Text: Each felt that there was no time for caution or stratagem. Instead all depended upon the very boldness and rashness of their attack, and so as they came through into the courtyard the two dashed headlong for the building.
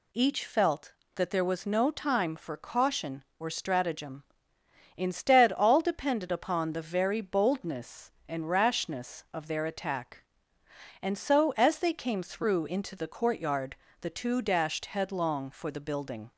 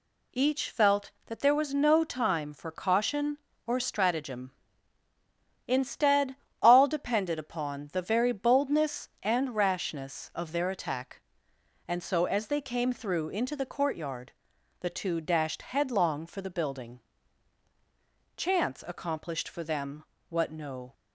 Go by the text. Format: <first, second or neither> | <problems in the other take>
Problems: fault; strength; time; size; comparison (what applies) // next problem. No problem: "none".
first | pauses between "Instead" and "all"; slight; at 6.3 s; 0.26 s long // pauses between "courtyard" and "the"; noticeable; at 14.3 s; 0.48 s long; slight in the first // goes on to say "Chance accomplished for them what no"; strong; from 18.3 s on; 2.5 s long